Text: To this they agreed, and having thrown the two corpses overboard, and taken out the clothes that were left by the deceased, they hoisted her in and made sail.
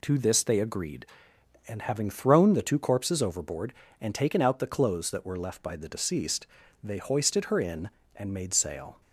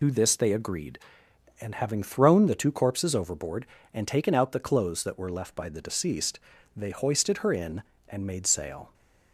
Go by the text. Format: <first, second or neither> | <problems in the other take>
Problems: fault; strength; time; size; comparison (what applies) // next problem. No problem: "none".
first | loses the start of "To"; at 0.0 s; 60 ms